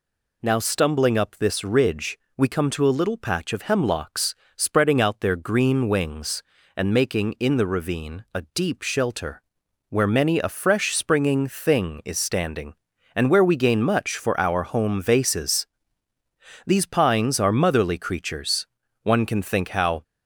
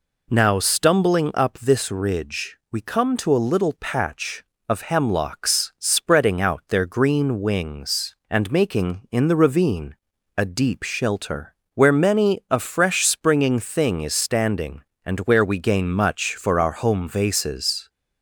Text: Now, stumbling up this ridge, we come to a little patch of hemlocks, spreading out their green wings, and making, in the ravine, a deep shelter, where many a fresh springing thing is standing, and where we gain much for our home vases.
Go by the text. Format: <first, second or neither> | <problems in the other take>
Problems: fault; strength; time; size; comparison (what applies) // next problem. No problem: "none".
second | goes on to say "These pines are motherly creatures One can think how"; strong; from 16.6 s on; 3.3 s long